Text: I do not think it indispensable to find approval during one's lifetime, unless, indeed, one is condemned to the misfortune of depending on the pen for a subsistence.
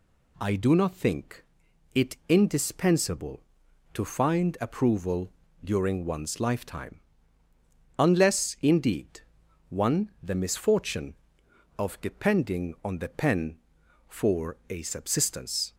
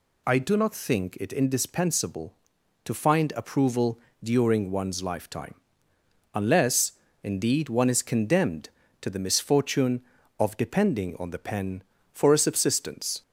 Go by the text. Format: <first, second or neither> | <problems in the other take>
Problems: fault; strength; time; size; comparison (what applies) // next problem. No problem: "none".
second | pauses between "think" and "it"; noticeable; at 1.4 s; 0.50 s long // pauses between "approval" and "during"; slight; at 5.3 s; 0.32 s long; slight in the second // skips "is condemned to"; at 10.1 s